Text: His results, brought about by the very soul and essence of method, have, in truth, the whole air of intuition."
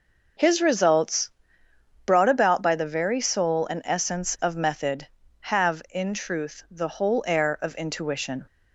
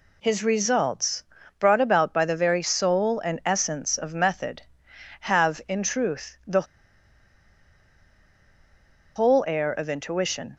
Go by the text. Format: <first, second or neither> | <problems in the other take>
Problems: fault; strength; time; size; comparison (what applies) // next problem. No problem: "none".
first | pauses between "the" and "whole"; strong; at 6.6 s; 2.5 s long